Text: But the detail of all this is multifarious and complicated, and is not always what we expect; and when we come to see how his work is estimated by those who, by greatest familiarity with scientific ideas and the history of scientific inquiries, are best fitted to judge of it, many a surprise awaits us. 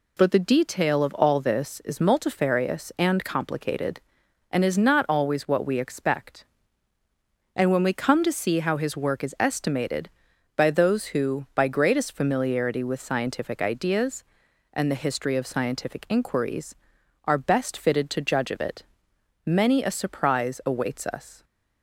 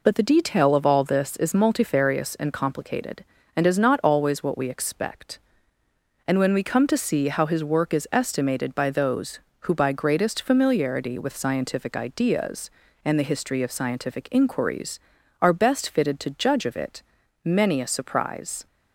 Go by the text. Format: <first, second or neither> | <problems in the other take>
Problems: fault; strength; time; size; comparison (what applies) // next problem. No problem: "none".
first | stops before "awaits us"; at 18.6 s